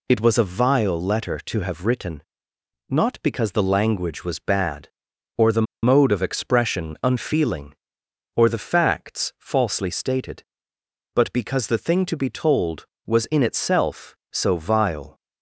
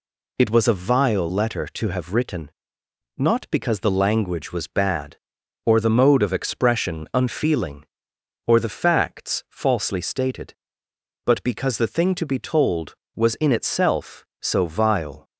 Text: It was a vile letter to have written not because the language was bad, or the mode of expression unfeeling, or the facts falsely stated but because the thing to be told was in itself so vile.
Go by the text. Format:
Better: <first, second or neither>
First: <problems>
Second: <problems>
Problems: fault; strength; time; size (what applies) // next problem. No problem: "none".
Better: second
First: pauses between "written" and "not"; noticeable; at 2.2 s; 0.66 s long // pauses between "the" and "mode"; slight; at 5.6 s; 0.19 s long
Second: pauses between "written" and "not"; noticeable; at 2.4 s; 0.66 s long